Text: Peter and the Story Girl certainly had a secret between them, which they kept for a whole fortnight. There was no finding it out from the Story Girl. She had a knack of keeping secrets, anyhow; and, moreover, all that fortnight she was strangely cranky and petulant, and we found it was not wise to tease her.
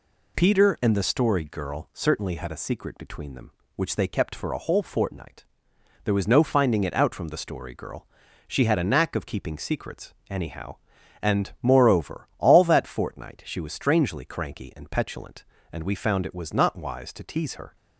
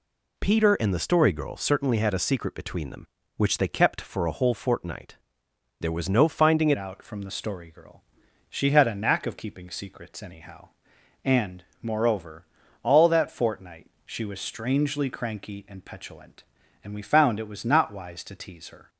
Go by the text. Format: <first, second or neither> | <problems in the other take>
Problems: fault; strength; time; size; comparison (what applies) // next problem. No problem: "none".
first | changes voice at "out"; from 6.7 s on; 12.1 s long // pauses between "fortnight" and "she"; slight; at 13.8 s; 0.18 s long